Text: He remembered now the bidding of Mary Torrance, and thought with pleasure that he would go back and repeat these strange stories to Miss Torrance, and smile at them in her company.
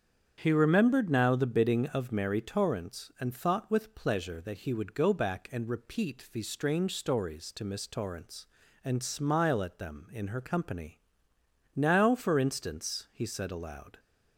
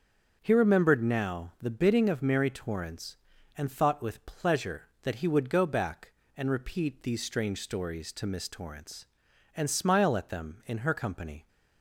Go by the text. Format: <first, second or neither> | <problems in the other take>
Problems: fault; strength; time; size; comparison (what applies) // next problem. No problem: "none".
second | starts louder than the rest; strong; until 1.4 s; 7.5 dB; also in the second // goes on to say "Now for instance he said aloud"; strong; from 11.7 s on; 2.2 s long